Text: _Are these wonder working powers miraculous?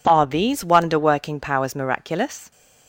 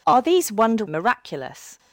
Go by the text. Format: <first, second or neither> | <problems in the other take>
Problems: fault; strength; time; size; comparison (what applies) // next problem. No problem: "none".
first | skips "working powers"; at 0.8 s